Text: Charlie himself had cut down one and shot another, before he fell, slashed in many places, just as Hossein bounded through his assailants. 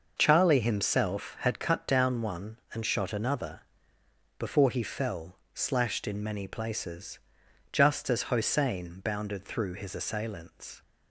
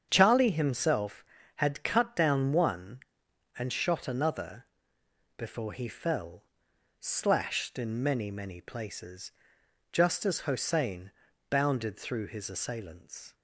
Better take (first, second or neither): first